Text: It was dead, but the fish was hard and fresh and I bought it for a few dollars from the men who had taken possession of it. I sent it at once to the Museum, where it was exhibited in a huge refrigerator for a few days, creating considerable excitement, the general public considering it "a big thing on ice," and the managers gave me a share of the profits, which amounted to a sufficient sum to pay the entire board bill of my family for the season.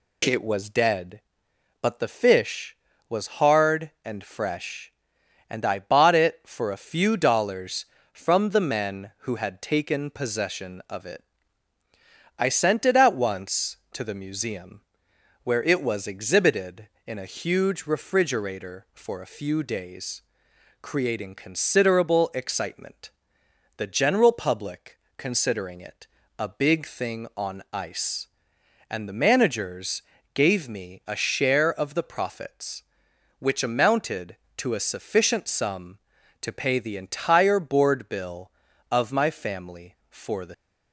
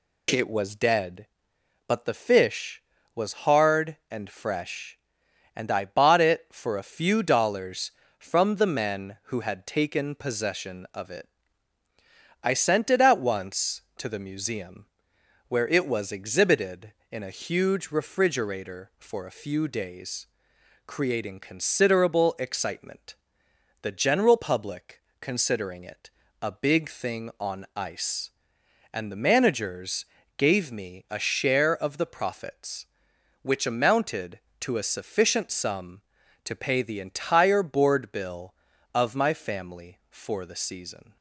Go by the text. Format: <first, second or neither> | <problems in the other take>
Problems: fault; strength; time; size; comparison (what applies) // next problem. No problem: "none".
second | pauses between "public" and "considering"; slight; at 24.9 s; 0.20 s long; slight in the second // pauses between "it" and "a"; slight; at 26.0 s; 0.32 s long; slight in the second // pauses between "managers" and "gave"; slight; at 30.0 s; 0.32 s long; slight in the second // stops before "season"; at 40.5 s